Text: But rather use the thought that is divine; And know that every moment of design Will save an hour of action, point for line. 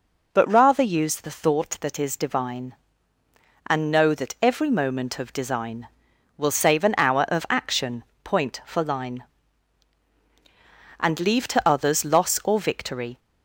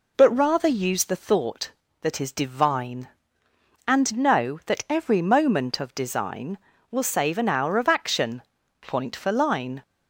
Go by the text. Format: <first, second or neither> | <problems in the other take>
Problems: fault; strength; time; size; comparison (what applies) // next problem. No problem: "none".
second | goes on to say "And leave to others loss or victory"; strong; from 11.0 s on; 2.1 s long